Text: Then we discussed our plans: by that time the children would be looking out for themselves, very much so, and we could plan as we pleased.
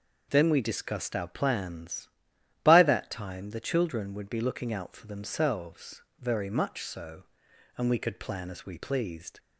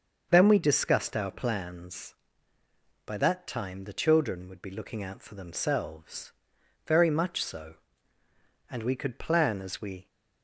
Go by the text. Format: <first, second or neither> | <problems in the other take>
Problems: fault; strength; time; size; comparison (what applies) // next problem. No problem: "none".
first | starts louder than the rest; until 1.3 s; 6.5 dB // stops before "pleased"; at 10.0 s